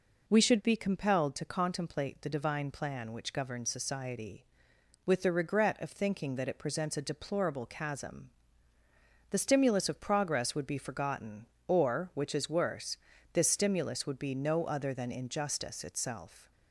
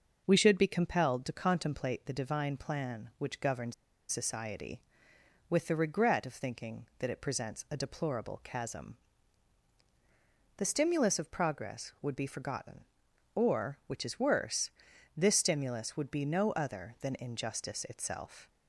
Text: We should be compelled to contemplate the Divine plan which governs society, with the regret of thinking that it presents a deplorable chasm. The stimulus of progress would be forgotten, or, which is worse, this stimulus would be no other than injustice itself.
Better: first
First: none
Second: pauses between "governs" and "society"; slight; at 3.7 s; 0.36 s long

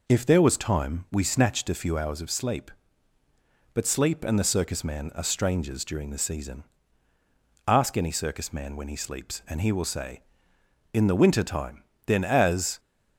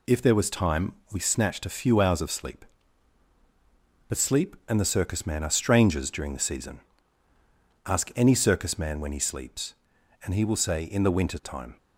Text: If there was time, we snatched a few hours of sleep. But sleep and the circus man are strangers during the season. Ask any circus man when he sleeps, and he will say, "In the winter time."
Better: second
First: goes on to say "Then as"; noticeable; from 12.0 s on; 0.74 s long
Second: none

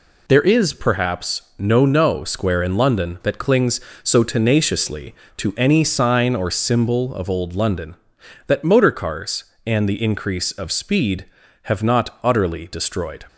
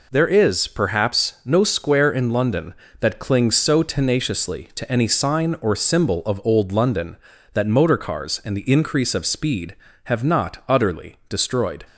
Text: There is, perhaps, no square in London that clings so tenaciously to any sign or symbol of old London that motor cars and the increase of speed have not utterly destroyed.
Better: second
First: says "no" twice; at 1.8 s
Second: none

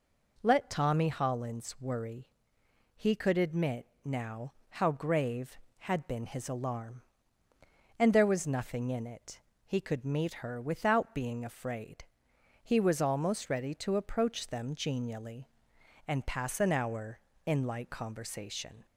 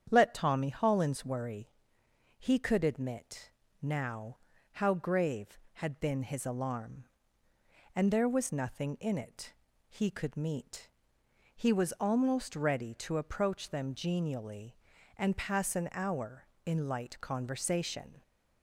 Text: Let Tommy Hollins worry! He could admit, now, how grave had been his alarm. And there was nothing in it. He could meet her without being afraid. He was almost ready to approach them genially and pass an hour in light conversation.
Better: first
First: none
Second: starts louder than the rest; strong; until 1.1 s; 8.5 dB // skips "her without being afraid"; at 11.2 s

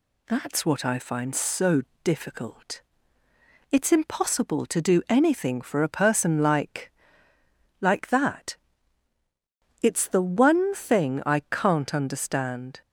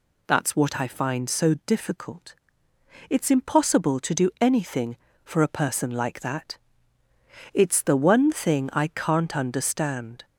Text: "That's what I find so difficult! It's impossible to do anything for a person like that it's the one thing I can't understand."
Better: second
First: pauses between "so" and "difficult"; slight; at 1.8 s; 0.24 s long // says "like" twice; at 7.7 s // pauses between "that" and "it's"; strong; at 8.5 s; 1.2 s long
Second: pauses between "that" and "it's"; noticeable; at 6.5 s; 0.96 s long

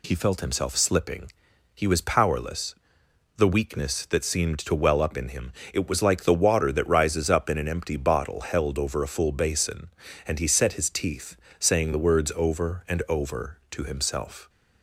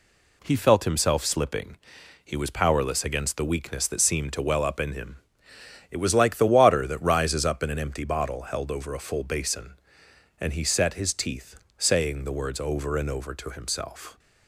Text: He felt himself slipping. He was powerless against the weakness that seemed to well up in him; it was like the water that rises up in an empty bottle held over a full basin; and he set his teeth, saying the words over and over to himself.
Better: second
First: skips "against"; at 3.0 s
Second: none

